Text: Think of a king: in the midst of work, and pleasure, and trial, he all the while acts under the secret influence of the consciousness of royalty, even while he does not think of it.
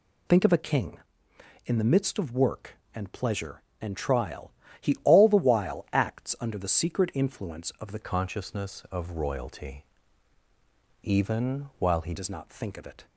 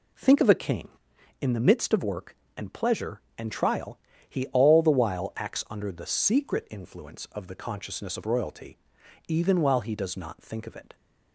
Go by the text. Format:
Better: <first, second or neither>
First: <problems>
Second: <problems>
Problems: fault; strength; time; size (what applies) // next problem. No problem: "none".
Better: second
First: changes voice from "consciousness" to "he"; from 8.0 to 12.1 s; 4.1 s long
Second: none